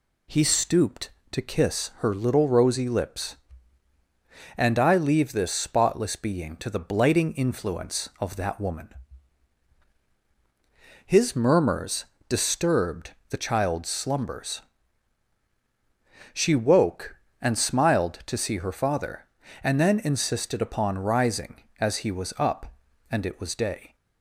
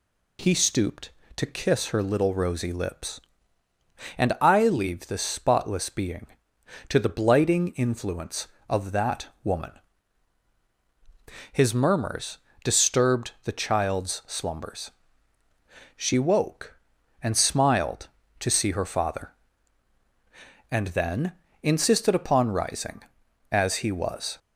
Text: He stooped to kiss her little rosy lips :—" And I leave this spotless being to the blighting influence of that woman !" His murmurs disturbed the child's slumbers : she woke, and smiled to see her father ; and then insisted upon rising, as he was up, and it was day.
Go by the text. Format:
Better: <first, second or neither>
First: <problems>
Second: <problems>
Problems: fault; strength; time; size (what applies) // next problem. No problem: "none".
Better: first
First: pauses between "murmurs" and "disturbed"; slight; at 12.0 s; 0.24 s long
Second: pauses between "that" and "woman"; slight; at 9.2 s; 0.16 s long // pauses between "murmurs" and "disturbed"; slight; at 12.3 s; 0.26 s long // pauses between "then" and "insisted"; slight; at 21.3 s; 0.28 s long // stops before "up and it was day"; at 24.3 s